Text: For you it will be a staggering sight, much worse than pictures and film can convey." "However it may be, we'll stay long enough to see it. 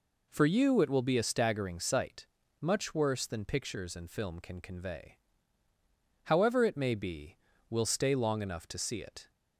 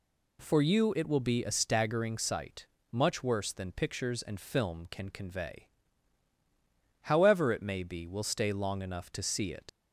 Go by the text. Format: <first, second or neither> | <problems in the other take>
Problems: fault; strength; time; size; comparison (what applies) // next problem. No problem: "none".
first | leaves "it" unfinished; at 9.6 s; 65 ms